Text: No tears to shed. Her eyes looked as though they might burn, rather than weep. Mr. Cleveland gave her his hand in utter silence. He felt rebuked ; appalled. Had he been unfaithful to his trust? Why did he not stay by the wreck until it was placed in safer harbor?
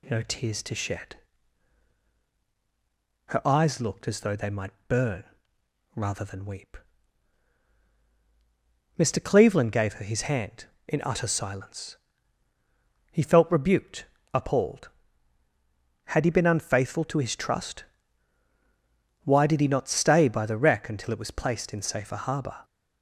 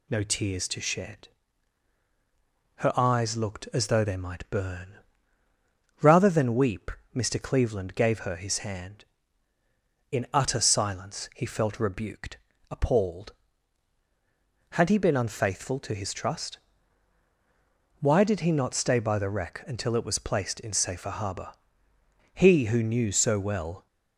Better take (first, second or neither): first